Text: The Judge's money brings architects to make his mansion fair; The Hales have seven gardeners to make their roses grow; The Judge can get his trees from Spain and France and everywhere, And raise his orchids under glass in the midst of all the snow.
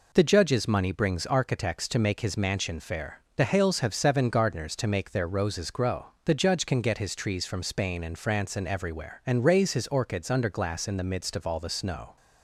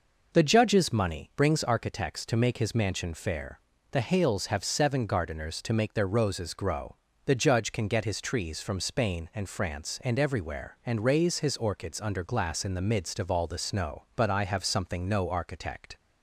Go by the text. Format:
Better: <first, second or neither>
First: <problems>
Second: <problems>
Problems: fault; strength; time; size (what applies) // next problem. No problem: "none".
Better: first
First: none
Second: goes on to say "But I have something no architect"; strong; from 14.1 s on; 1.8 s long